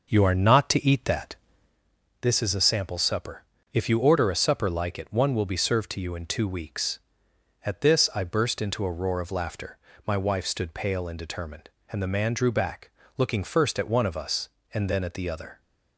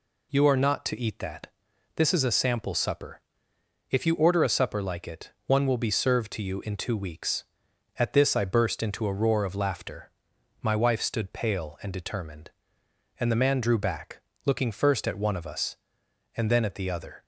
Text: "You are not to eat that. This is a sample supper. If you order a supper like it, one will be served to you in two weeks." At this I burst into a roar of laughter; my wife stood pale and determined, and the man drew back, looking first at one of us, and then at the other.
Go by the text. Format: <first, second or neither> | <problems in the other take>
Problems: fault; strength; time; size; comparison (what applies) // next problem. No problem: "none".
second | starts louder than the rest; noticeable; until 1.9 s; 6 dB